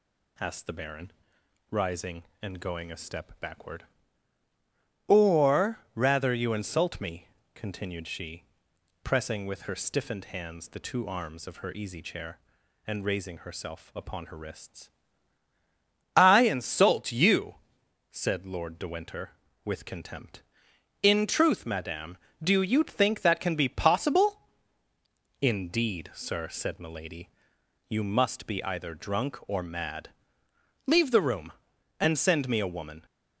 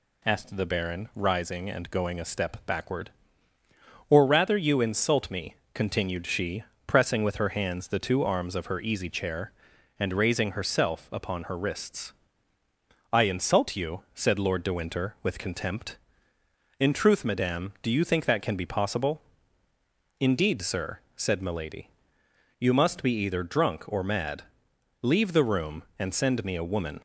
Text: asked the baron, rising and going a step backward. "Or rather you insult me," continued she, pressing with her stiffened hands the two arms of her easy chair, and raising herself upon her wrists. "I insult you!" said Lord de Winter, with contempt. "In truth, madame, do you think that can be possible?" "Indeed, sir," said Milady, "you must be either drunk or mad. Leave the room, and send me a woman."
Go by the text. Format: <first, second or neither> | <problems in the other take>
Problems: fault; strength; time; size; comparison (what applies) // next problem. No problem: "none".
first | skips "stiffened"; at 7.5 s